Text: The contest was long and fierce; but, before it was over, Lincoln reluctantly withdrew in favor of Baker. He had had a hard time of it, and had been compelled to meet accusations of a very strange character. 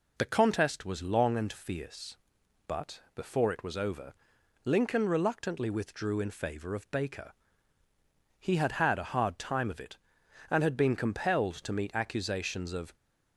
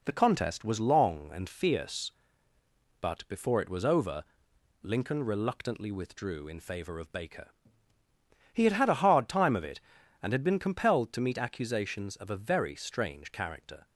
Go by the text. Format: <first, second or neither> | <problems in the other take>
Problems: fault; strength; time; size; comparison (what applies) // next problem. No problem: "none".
second | stops before "a very strange character"; at 12.9 s